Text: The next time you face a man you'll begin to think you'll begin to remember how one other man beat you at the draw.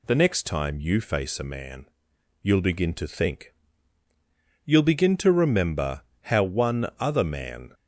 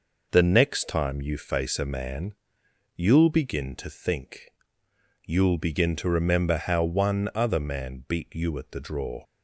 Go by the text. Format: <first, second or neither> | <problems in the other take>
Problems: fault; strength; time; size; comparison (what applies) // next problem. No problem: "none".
second | pauses between "man" and "you'll"; noticeable; at 1.8 s; 0.56 s long; noticeable in the second // pauses between "think" and "you'll"; at 3.5 s; 1.0 s long; noticeable in the second // pauses between "remember" and "how"; slight; at 6.0 s; 0.18 s long // stops before "beat you at the draw"; at 7.7 s